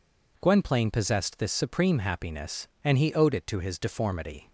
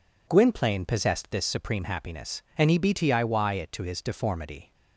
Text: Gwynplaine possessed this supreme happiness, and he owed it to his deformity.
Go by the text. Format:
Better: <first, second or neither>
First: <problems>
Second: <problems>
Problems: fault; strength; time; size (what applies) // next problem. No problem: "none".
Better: first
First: none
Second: says "btiy" for "owed"; at 2.7 s